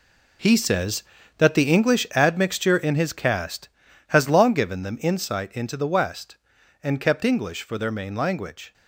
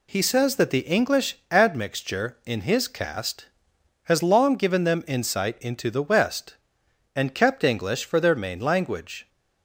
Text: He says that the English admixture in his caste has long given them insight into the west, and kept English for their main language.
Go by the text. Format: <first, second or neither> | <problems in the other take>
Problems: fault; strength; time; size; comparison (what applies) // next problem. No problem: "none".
second | gets quieter; strong; throughout; 11.5 dB